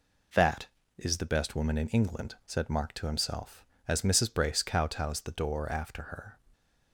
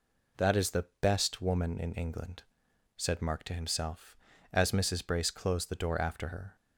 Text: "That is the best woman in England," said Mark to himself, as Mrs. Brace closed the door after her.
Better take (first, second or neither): second